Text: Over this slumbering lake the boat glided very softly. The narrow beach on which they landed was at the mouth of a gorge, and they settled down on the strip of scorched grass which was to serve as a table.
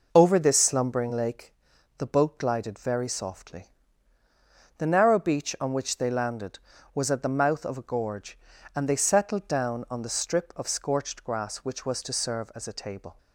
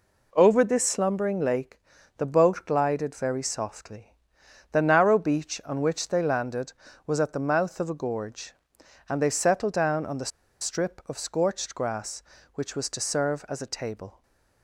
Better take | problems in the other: first | pauses between "lake" and "the"; at 1.7 s; 0.38 s long; noticeable in the first // pauses between "the" and "strip"; slight; at 10.3 s; 0.31 s long // stays silent after the last word; slight; from 14.1 s on; 0.5 s long

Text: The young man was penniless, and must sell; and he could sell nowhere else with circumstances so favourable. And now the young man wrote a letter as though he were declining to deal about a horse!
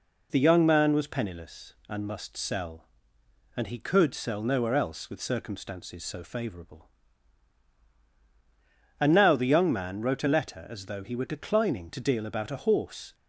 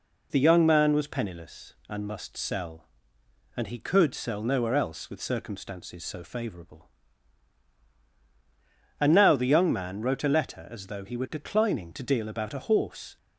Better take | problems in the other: neither | none

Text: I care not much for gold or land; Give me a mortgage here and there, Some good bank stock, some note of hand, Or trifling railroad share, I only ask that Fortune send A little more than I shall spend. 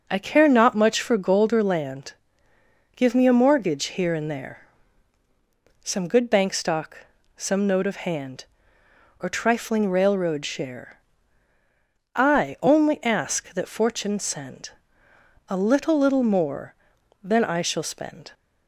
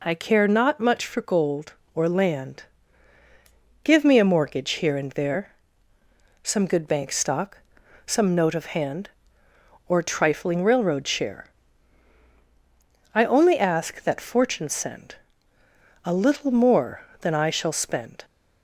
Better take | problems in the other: second | pauses between "send" and "A"; noticeable; at 14.6 s; 0.80 s long; noticeable in the second // says "little" twice; at 15.9 s

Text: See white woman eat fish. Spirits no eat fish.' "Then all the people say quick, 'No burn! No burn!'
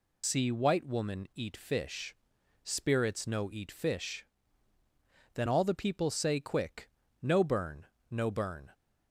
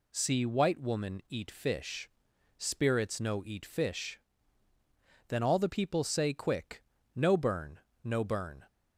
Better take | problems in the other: second | loses the start of "See"; at 0.2 s; 55 ms

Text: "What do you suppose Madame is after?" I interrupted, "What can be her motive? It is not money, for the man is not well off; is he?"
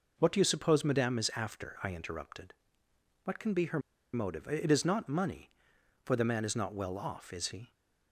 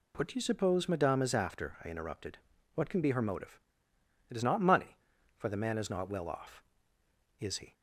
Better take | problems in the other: second | pauses between "her" and "motive"; slight; at 3.7 s; 0.35 s long

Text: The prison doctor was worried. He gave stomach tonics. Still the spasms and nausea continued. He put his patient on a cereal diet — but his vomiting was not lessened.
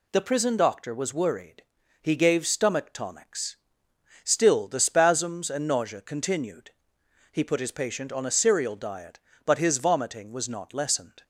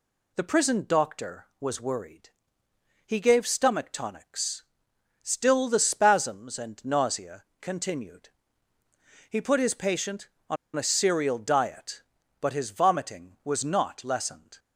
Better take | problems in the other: first | pauses between "nausea" and "continued"; slight; at 7.4 s; 0.18 s long // pauses between "on" and "a"; slight; at 10.5 s; 0.20 s long

